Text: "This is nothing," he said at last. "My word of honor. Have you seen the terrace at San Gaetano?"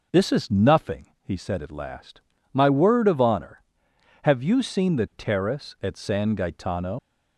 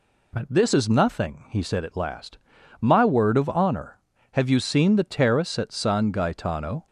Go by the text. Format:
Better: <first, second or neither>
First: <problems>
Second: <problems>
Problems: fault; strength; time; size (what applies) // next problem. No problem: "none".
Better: second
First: leaves "Gaetano" unfinished; at 6.9 s; 80 ms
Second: none